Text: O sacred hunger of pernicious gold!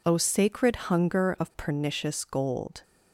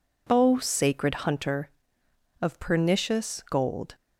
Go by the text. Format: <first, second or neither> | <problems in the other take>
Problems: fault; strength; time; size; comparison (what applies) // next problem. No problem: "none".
first | says "hunter" for "hunger"; at 1.1 s